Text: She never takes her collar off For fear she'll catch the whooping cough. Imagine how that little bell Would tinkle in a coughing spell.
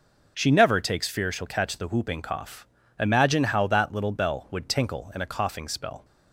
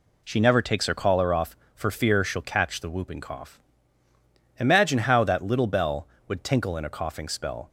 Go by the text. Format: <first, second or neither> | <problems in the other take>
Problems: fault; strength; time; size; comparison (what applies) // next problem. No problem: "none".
second | skips "her collar off For"; at 1.0 s